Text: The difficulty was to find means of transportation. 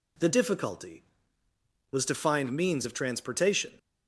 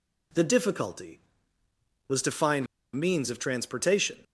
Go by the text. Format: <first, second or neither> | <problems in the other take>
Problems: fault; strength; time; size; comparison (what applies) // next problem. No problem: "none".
first | pauses between "find" and "means"; slight; at 2.6 s; 0.30 s long